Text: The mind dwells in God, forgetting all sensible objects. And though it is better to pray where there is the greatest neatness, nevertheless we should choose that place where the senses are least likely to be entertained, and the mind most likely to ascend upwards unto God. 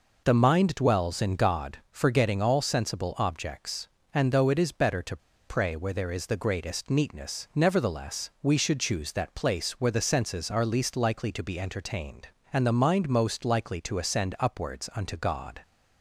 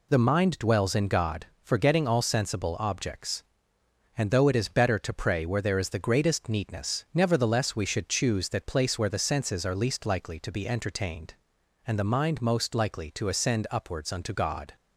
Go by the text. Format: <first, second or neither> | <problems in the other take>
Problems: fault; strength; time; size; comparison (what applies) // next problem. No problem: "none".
second | pauses between "to" and "pray"; slight; at 5.1 s; 0.31 s long